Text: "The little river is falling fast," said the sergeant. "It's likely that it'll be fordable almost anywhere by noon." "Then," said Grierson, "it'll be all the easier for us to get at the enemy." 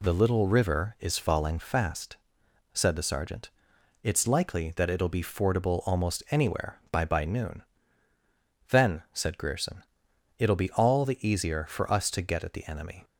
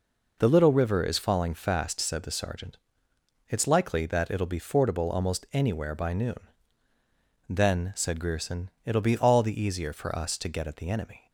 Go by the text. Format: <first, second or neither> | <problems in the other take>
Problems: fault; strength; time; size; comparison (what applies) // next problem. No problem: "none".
second | says "by" twice; at 7.0 s